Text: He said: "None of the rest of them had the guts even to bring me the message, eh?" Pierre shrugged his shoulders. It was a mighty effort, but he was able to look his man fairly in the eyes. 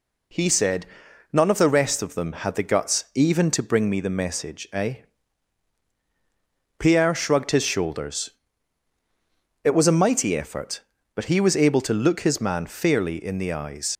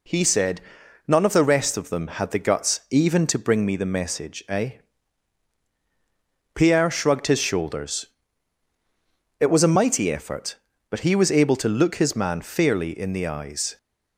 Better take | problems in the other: second | leaves "eyes" unfinished; at 13.9 s; 75 ms

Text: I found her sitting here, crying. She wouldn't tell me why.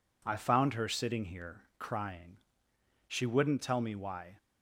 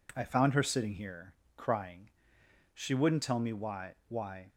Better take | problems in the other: first | says "why" twice; at 4.0 s

